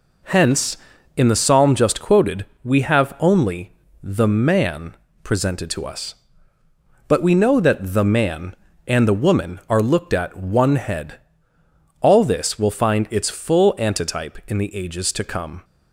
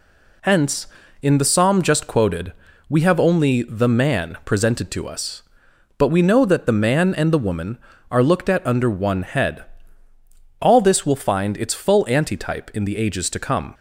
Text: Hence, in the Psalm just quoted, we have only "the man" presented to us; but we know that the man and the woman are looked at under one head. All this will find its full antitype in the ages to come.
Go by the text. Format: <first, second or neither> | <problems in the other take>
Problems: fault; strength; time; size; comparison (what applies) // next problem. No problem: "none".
second | pauses between "only" and "the"; slight; at 3.7 s; 0.30 s long // pauses between "man" and "presented"; slight; at 4.9 s; 0.26 s long // skips "under"; at 10.3 s